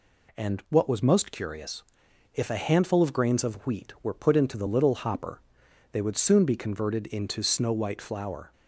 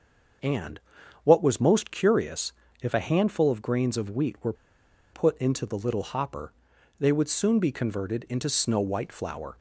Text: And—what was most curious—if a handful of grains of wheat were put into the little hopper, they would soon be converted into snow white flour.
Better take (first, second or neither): first